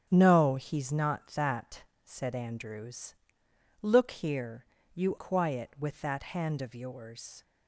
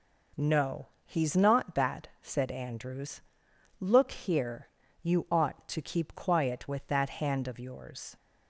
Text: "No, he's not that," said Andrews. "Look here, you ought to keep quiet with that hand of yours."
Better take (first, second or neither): second